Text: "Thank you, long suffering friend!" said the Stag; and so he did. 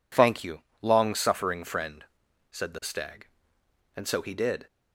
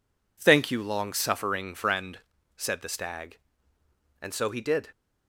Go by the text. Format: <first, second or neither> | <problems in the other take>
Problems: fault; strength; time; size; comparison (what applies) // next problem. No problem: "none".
neither | none